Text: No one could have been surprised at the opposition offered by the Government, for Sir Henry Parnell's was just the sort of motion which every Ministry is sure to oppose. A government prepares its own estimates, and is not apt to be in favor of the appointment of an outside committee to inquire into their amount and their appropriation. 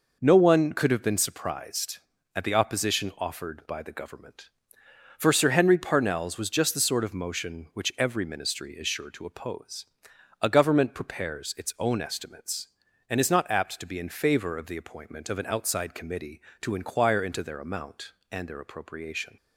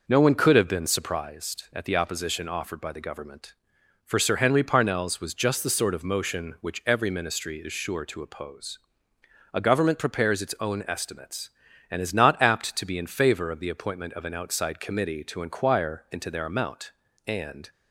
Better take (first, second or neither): first